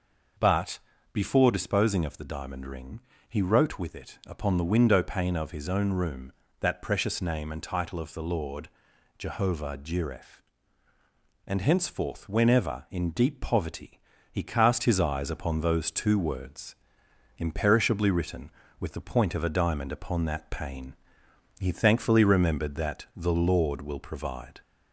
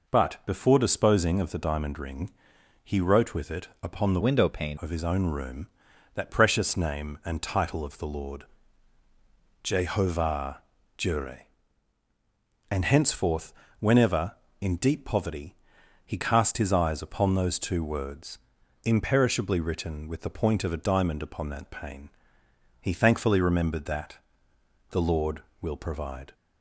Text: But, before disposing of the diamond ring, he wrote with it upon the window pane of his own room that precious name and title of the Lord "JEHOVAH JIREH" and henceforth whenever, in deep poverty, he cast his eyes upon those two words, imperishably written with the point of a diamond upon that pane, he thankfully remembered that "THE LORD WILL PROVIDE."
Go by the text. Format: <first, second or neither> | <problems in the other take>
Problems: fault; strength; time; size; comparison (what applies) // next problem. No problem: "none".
first | pauses between "it" and "upon"; slight; at 3.6 s; 0.16 s long // changes voice from "window" to "pane"; from 4.2 to 4.7 s; 0.5 s long // pauses between "Lord" and "JEHOVAH"; at 8.4 s; 1.1 s long; noticeable in the first // pauses between "JEHOVAH" and "JIREH"; slight; at 10.6 s; 0.34 s long // pauses between "henceforth" and "whenever"; slight; at 13.5 s; 0.26 s long // pauses between "that" and "THE"; noticeable; at 24.1 s; 0.72 s long